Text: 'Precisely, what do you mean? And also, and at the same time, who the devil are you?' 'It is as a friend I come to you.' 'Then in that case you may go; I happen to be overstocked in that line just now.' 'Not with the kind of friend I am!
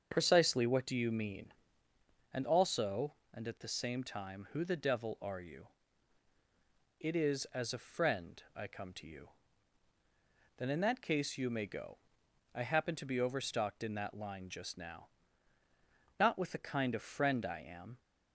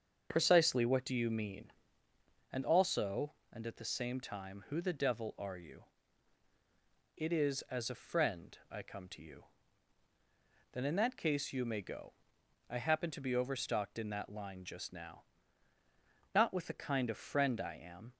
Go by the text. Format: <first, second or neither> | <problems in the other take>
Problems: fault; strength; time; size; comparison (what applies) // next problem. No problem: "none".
neither | starts louder than the rest; the same in both